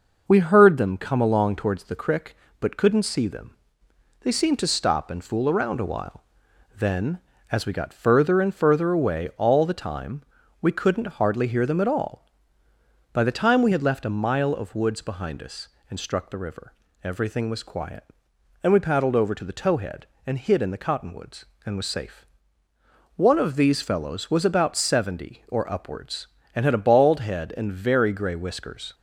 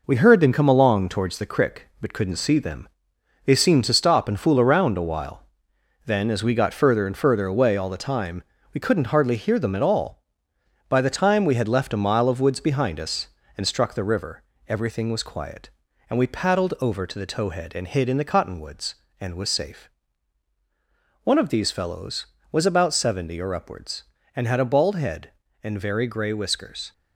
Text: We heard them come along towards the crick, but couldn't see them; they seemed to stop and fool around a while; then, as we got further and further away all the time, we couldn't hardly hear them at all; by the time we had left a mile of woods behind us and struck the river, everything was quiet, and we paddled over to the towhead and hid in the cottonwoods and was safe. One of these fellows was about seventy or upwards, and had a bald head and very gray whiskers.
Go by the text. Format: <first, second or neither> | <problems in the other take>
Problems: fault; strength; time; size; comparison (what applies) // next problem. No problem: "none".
first | gets quieter; throughout; 6.5 dB